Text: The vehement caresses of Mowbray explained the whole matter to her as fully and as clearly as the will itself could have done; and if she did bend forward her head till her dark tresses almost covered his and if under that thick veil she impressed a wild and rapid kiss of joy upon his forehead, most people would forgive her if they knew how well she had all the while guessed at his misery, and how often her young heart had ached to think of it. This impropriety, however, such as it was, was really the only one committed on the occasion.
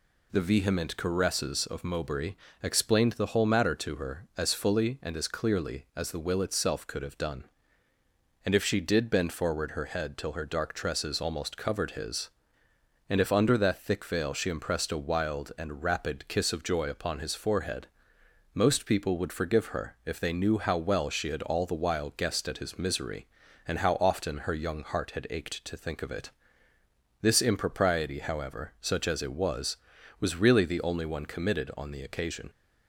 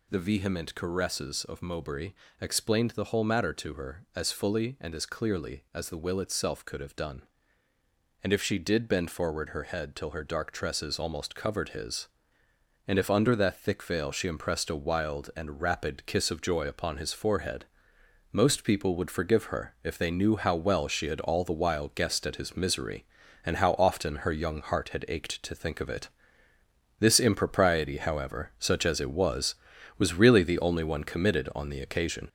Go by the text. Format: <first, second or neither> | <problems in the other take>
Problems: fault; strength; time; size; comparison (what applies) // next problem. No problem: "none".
first | gets louder; noticeable; throughout; 5 dB // pauses between "Mowbray" and "explained"; slight; at 2.1 s; 0.26 s long; slight in the first